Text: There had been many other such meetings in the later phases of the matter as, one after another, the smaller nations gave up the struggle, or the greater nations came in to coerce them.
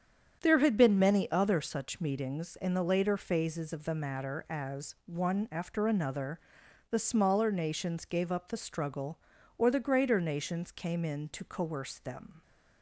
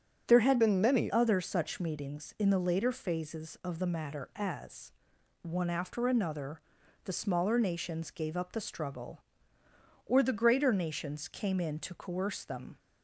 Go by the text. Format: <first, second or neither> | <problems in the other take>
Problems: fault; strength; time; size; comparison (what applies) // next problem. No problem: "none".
first | starts louder than the rest; strong; until 1.2 s; 8 dB; strong in the first // changes voice from "been" to "many"; from 0.5 to 1.0 s; 0.5 s long